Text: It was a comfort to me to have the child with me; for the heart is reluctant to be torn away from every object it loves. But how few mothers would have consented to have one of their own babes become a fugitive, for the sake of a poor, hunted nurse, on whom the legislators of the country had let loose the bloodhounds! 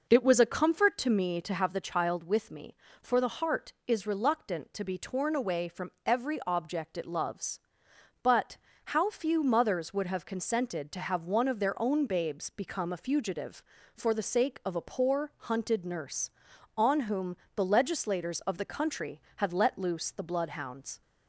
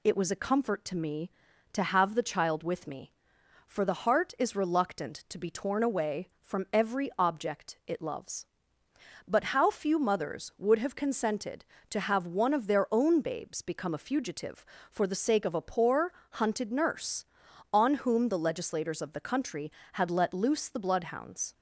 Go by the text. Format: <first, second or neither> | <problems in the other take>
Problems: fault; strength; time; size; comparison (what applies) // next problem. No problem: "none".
second | starts louder than the rest; noticeable; until 1.8 s; 5 dB // pauses between "But" and "how"; at 8.5 s; 0.40 s long // pauses between "whom" and "the"; slight; at 17.3 s; 0.22 s long